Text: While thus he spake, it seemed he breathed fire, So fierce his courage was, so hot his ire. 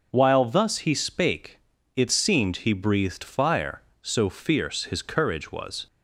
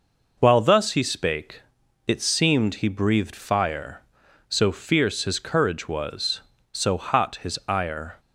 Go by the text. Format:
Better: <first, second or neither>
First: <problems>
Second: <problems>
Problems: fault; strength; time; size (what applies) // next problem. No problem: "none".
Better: second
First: stops before "so hot his ire"; at 5.8 s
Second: none